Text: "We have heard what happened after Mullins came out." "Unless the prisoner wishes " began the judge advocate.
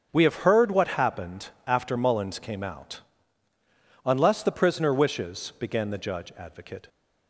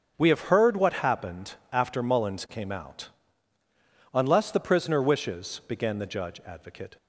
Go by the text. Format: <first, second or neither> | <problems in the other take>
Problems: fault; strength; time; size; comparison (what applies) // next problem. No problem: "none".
neither | starts louder than the rest; strong; the same in both // pauses between "happened" and "after"; slight; the same in both